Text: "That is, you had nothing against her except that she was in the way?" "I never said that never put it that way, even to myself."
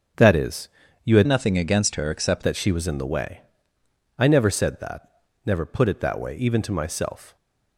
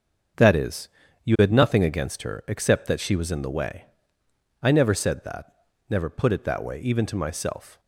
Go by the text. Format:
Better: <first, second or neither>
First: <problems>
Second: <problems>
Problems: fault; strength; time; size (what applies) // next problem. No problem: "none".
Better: second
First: starts louder than the rest; until 1.5 s; 6.5 dB // changes voice from "nothing" to "except"; from 1.2 to 2.4 s; 1.2 s long // pauses between "that" and "never"; at 5.0 s; 0.38 s long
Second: starts louder than the rest; until 1.7 s; 6.5 dB // pauses between "that" and "never"; at 5.5 s; 0.38 s long